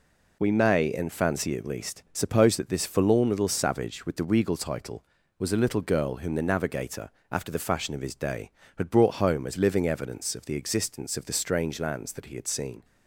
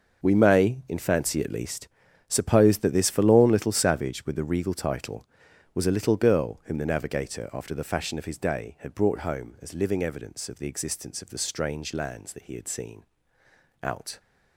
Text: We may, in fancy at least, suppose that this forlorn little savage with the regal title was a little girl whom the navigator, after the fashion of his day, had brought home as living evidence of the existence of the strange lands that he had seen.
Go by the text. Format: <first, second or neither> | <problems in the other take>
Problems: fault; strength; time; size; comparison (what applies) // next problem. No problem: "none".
first | starts louder than the rest; noticeable; until 1.2 s; 6 dB // goes on to say "Out"; slight; from 13.8 s on; 0.38 s long